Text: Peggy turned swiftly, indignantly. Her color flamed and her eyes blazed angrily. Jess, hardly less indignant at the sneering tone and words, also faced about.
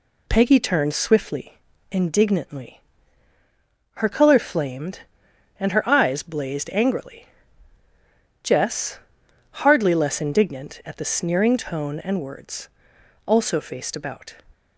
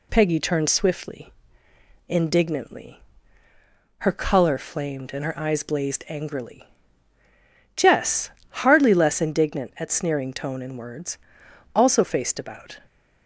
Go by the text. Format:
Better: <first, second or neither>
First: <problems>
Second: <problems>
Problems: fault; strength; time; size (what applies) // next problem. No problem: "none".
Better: first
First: none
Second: skips "the"; at 9.9 s